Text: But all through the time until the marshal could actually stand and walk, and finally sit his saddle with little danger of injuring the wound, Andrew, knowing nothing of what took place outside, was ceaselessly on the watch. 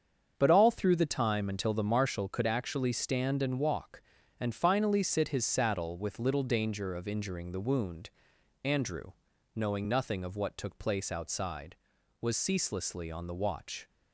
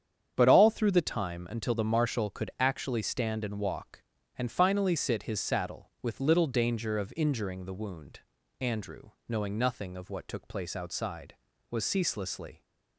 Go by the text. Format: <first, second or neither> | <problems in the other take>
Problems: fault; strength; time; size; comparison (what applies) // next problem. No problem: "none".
first | starts louder than the rest; strong; until 1.3 s; 8.5 dB; strong in the first // stops before "on the watch"; at 12.6 s